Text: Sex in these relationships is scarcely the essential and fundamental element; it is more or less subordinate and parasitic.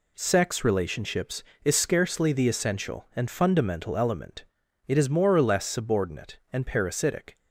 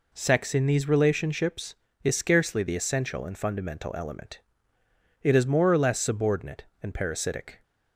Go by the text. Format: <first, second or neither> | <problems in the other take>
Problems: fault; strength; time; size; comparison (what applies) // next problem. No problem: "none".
second | skips "in these"; at 0.6 s